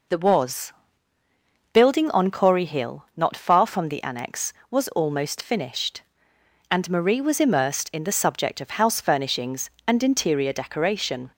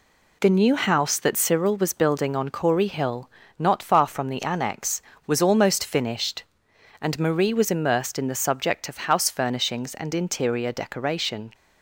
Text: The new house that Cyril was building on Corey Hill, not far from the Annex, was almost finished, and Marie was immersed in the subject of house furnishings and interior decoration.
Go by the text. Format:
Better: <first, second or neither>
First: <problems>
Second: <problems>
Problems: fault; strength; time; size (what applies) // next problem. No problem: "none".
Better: second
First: skips "new house that Cyril"; at 0.1 s // pauses between "was" and "building"; noticeable; at 0.7 s; 0.98 s long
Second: none